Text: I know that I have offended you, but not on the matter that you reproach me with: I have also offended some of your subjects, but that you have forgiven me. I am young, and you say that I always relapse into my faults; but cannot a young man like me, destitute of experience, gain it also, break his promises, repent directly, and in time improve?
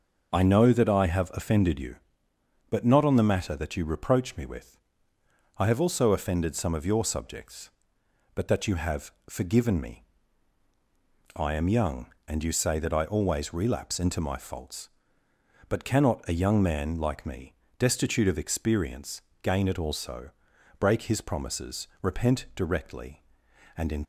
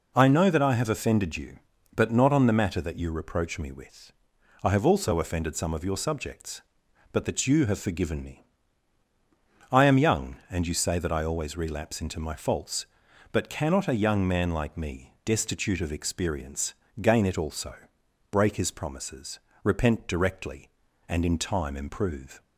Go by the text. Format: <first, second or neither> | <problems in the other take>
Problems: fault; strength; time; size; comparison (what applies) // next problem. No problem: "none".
second | pauses between "have" and "forgiven"; slight; at 9.1 s; 0.18 s long // stops before "time improve"; at 24.0 s